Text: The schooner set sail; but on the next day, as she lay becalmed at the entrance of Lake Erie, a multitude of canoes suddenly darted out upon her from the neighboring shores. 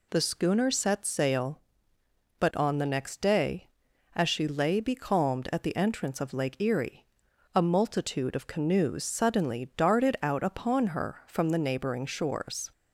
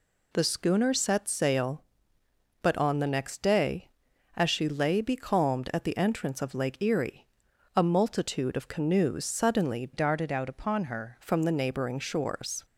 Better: first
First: none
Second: changes voice from "darted" to "her"; from 9.9 to 11.1 s; 1.2 s long

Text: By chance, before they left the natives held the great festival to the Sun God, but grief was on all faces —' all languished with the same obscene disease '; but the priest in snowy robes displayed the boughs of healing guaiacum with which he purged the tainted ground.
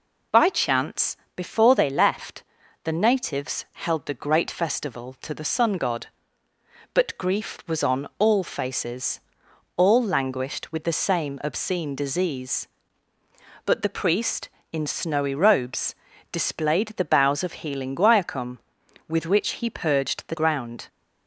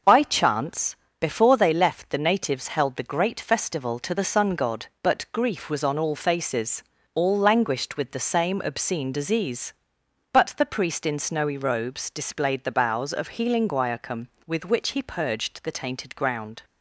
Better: second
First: pauses between "left" and "the"; at 2.4 s; 0.40 s long // pauses between "robes" and "displayed"; at 15.9 s; 0.38 s long // skips "tainted"; at 20.3 s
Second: none

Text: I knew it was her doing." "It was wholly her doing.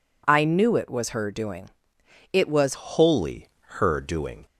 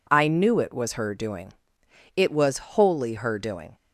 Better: second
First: changes voice at "wholly"; from 2.7 s on; 1.7 s long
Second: none

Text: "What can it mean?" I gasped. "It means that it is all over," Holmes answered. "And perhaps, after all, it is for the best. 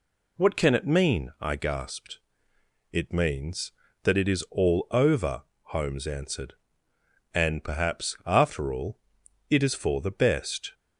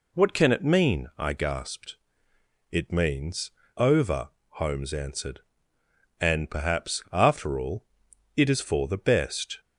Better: first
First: none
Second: skips "that it is all"; at 3.6 s

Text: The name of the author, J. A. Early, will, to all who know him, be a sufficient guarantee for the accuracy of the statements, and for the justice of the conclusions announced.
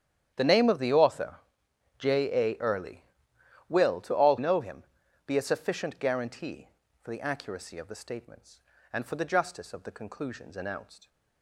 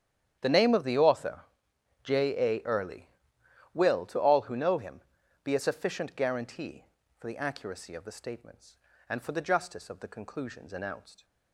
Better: second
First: starts louder than the rest; strong; until 2.0 s; 9.5 dB // skips "who"; at 4.3 s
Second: starts louder than the rest; strong; until 2.0 s; 9.5 dB

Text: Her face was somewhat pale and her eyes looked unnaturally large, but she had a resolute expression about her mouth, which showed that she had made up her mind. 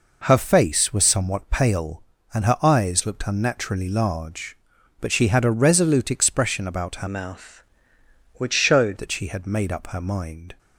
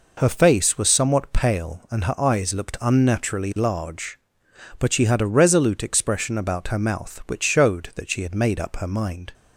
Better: second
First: changes voice from "mouth" to "showed"; from 7.0 to 8.9 s; 1.9 s long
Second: none

